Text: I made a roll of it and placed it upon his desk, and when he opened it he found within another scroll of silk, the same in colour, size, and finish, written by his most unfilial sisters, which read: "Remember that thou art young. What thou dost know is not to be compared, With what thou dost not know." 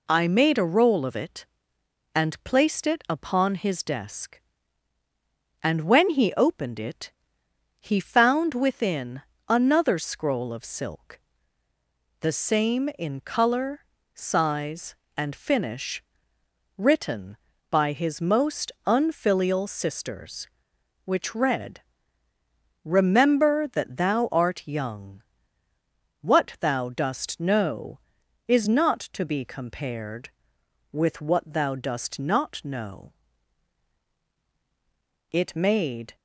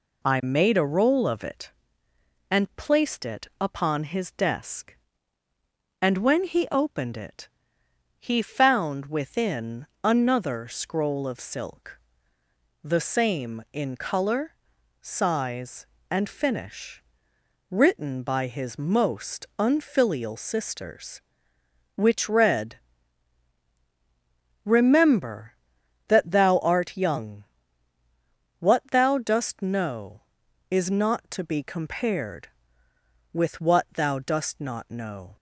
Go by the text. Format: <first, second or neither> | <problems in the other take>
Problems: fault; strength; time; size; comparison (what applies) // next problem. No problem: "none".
second | pauses between "it" and "he"; noticeable; at 7.1 s; 0.70 s long; noticeable in the second // pauses between "within" and "another"; slight; at 9.2 s; 0.26 s long; slight in the second // goes on to say "It made"; noticeable; from 35.3 s on; 0.84 s long